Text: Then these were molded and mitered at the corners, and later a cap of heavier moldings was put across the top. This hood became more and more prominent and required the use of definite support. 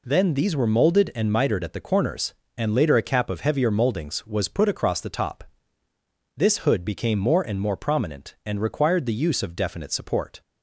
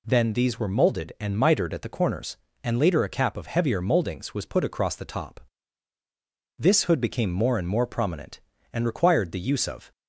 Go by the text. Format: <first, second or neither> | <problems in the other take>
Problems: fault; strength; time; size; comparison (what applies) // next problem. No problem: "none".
first | stops before "definite support"; at 9.9 s